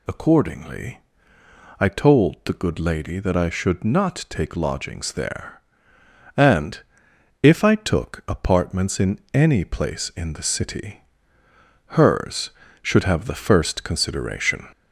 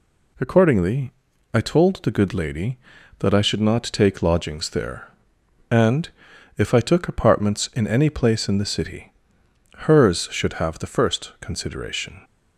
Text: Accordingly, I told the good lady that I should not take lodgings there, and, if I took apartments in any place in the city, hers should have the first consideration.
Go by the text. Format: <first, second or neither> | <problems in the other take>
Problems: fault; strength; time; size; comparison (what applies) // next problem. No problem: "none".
second | gets louder; slight; throughout; 2.5 dB // pauses between "in" and "any"; slight; at 9.1 s; 0.16 s long